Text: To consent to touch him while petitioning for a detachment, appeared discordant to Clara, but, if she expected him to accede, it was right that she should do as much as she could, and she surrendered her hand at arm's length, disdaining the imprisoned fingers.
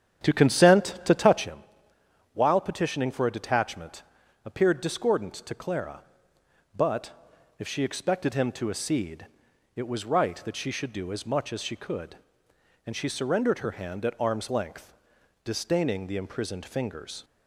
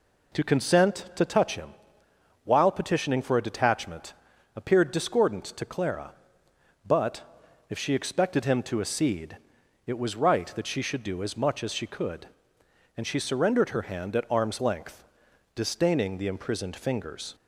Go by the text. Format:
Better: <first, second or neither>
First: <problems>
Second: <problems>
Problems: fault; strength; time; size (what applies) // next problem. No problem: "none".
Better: second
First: starts louder than the rest; strong; until 1.5 s; 8.5 dB // pauses between "him" and "while"; noticeable; at 1.6 s; 0.70 s long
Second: pauses between "him" and "while"; noticeable; at 1.7 s; 0.70 s long